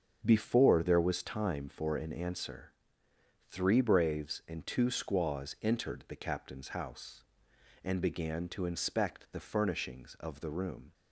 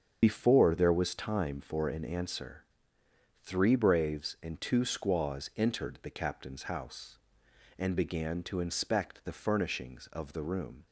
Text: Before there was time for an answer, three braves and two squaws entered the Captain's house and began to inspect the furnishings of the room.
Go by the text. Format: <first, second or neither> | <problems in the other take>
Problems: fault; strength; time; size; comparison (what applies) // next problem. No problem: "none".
first | loses the start of "Before"; at 0.2 s; 75 ms // starts louder than the rest; strong; until 1.2 s; 7 dB; strong in the first